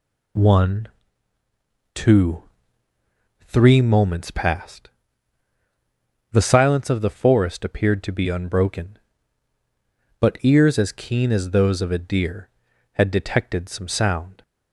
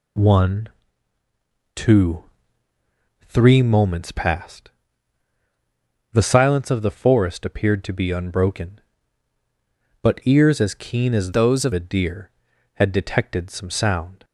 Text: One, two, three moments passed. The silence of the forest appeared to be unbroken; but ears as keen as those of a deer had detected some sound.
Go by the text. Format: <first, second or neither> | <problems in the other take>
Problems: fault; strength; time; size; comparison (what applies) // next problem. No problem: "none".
first | changes voice from "those" to "of"; from 11.3 to 11.7 s; 0.4 s long